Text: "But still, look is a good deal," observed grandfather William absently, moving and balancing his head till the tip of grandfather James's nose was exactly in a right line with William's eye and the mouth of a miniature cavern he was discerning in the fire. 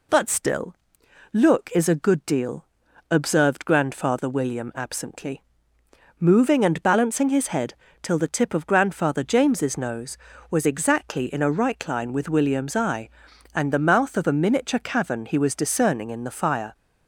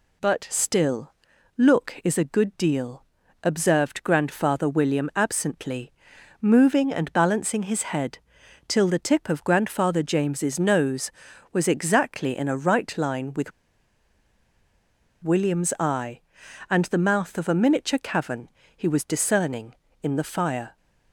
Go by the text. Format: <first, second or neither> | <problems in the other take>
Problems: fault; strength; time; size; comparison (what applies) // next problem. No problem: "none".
first | pauses between "head" and "till"; noticeable; at 8.1 s; 0.48 s long; slight in the first // pauses between "with" and "William's"; strong; at 13.5 s; 1.7 s long // pauses between "cavern" and "he"; slight; at 18.4 s; 0.28 s long